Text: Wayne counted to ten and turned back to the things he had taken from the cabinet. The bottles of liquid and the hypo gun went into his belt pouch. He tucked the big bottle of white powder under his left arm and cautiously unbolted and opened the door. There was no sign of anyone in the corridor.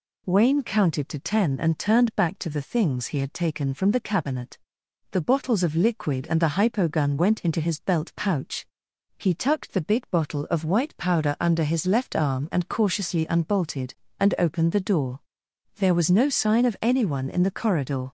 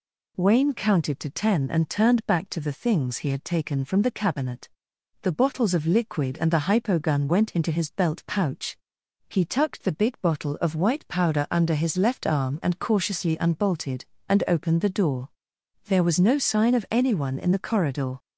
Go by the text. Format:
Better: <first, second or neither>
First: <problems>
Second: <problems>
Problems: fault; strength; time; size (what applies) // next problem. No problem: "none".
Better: neither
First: none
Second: none